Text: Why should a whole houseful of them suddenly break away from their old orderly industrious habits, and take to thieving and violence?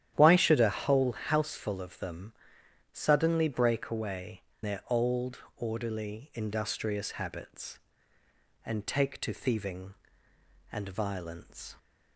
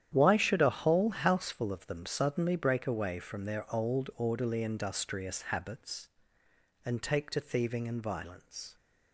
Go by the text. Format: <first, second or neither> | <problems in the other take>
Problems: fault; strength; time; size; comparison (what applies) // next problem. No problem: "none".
second | starts louder than the rest; strong; until 1.1 s; 11 dB; strong in the second // pauses between "them" and "suddenly"; noticeable; at 2.3 s; 0.62 s long // skips "from"; at 4.5 s // pauses between "old" and "orderly"; slight; at 5.3 s; 0.18 s long